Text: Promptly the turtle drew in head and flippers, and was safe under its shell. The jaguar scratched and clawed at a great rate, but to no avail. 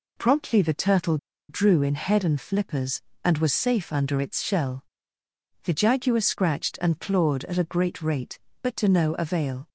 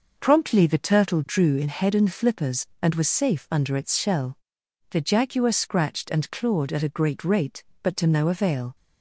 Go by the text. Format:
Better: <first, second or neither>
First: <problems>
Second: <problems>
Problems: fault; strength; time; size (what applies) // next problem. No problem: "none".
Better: second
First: pauses between "turtle" and "drew"; slight; at 1.1 s; 0.32 s long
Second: none